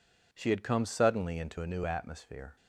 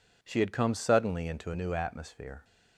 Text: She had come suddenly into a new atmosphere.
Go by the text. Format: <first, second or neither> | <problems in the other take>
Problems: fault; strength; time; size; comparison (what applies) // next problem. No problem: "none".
neither | none